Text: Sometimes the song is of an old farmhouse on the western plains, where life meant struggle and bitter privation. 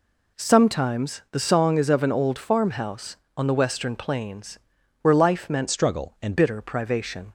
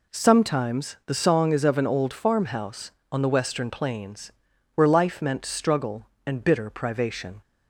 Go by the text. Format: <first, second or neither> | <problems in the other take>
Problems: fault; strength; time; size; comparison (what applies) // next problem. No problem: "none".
second | changes voice from "struggle" to "and"; from 5.6 to 6.3 s; 0.7 s long